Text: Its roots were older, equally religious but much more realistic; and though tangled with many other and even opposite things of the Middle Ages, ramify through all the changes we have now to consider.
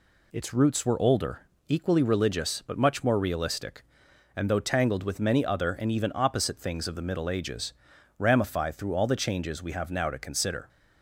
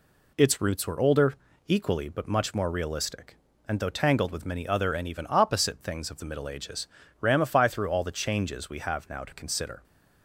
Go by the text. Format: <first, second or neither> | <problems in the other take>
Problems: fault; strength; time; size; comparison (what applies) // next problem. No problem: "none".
first | skips "religious"; at 2.0 s